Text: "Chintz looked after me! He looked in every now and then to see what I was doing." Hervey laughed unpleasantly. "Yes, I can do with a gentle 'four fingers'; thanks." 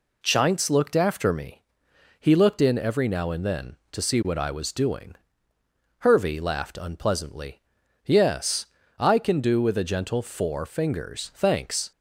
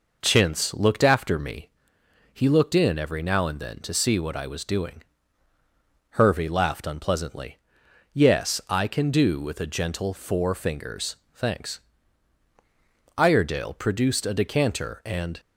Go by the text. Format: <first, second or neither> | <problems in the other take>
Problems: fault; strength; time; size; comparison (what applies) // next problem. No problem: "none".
first | goes on to say "Iredale produced a decanter and"; strong; from 13.1 s on; 2.2 s long